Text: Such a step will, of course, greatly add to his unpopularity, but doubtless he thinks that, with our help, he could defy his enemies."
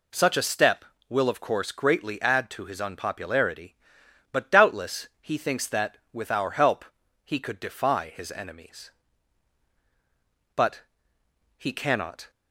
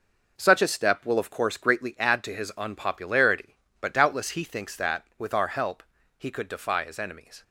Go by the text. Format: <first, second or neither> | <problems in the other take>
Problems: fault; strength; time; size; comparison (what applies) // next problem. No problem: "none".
second | goes on to say "But he cannot"; strong; from 10.5 s on; 1.7 s long